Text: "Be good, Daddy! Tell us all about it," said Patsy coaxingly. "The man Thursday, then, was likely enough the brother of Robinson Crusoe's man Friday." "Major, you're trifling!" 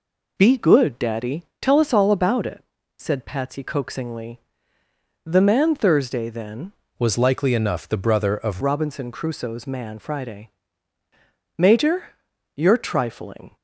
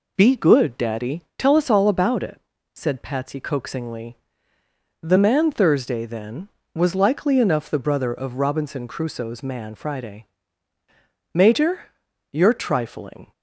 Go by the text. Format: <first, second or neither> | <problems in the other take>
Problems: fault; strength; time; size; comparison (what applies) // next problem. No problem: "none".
second | changes voice from "was" to "of"; from 6.9 to 8.6 s; 1.7 s long